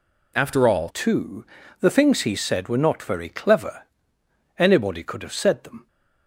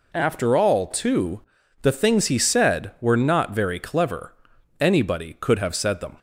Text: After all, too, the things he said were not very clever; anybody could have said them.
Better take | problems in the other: second | changes voice at "too"; from 0.8 s on; 5.0 s long

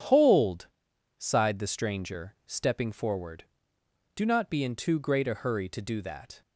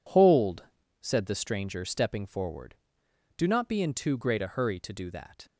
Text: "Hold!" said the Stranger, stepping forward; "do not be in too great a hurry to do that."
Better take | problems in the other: second | says "sighed" for "said"; at 1.1 s

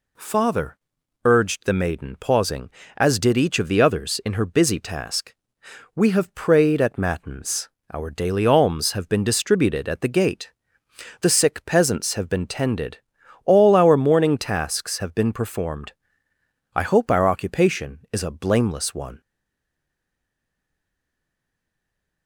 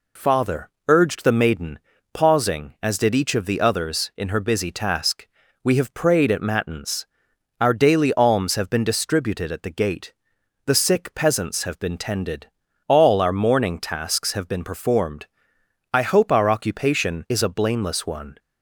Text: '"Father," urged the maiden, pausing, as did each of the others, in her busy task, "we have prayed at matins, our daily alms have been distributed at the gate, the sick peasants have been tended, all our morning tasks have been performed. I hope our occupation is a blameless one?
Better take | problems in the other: second | stays silent after the last word; strong; from 19.2 s on; 3.0 s long

